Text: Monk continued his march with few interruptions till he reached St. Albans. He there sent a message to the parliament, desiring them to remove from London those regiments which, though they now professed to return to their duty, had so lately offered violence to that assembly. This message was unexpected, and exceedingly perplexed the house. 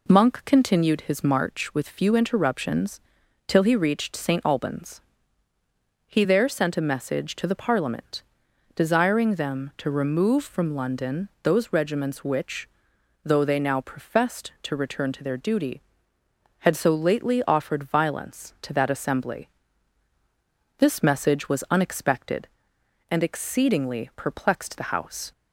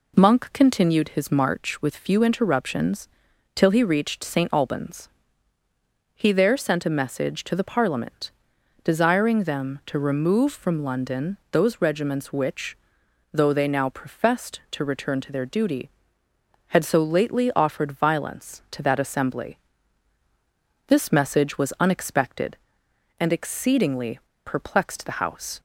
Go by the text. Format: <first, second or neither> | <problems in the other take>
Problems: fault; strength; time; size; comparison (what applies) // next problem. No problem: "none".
first | pauses between "interruptions" and "till"; noticeable; at 3.0 s; 0.48 s long; noticeable in the first // pauses between "exceedingly" and "perplexed"; slight; at 24.2 s; 0.25 s long